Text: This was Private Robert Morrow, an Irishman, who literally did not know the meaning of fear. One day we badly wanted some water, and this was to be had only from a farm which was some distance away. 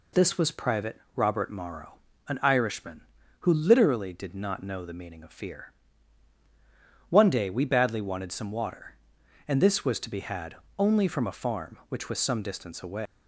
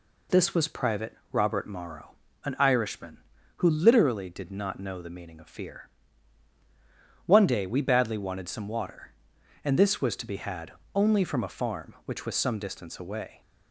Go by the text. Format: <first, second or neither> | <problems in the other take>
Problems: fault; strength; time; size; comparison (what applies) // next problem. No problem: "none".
second | pauses between "Private" and "Robert"; slight; at 1.0 s; 0.16 s long; slight in the second // pauses between "had" and "only"; slight; at 10.5 s; 0.24 s long; slight in the second // leaves "away" unfinished; at 13.0 s; 185 ms